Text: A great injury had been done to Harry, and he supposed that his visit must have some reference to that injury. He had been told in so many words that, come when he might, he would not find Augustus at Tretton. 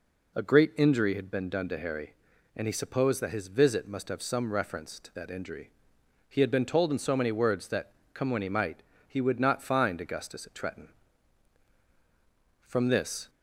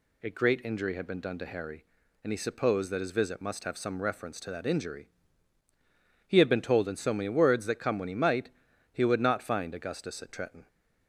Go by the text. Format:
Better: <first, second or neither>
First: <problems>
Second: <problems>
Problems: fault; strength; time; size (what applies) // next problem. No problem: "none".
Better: second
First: goes on to say "From this"; noticeable; from 12.6 s on; 0.62 s long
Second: none